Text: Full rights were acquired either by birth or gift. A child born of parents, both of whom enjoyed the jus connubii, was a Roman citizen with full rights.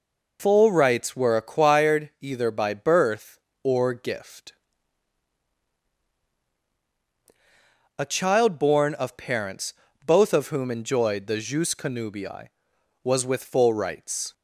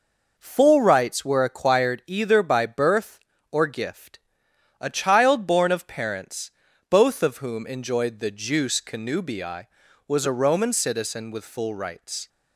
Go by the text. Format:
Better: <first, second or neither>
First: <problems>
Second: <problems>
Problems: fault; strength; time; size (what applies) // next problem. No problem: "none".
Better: second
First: skips "a Roman citizen"; at 13.2 s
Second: none